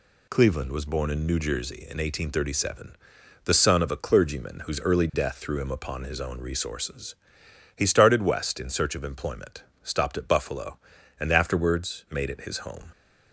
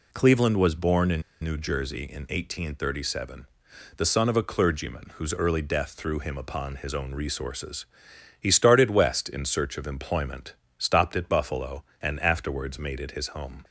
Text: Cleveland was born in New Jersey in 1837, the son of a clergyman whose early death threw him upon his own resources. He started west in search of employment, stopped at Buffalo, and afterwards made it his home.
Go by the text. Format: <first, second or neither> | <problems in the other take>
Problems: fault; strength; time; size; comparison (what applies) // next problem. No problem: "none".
first | pauses between "in" and "New"; slight; at 1.2 s; 0.19 s long